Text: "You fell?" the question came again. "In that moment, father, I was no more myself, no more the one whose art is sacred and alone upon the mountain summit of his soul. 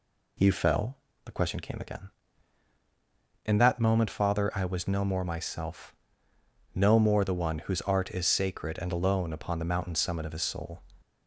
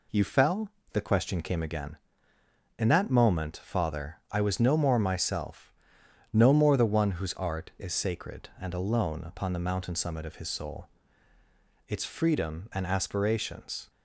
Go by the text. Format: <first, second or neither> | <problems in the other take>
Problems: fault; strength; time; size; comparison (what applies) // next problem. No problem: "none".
first | goes on to say "Its freedom and aspirations"; strong; from 11.8 s on; 2.0 s long